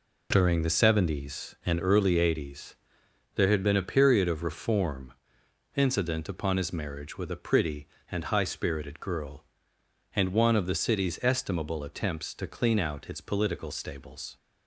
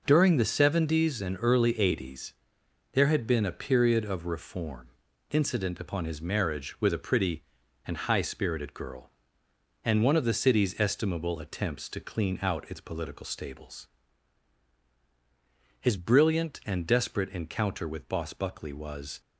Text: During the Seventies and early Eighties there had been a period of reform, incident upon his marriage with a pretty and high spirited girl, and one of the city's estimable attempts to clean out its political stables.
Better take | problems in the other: first | pauses between "Eighties" and "there"; noticeable; at 2.3 s; 0.58 s long; noticeable in the first // goes on to say "His brilliant and desperate encounter with Boss Buckley was"; strong; from 15.7 s on; 3.4 s long

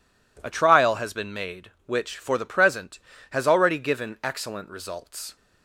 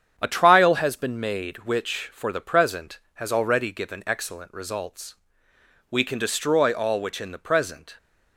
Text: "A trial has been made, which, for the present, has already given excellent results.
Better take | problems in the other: first | starts louder than the rest; strong; until 1.1 s; 8.5 dB // goes on to say "We can destroy all which in the present"; strong; from 5.9 s on; 2.0 s long

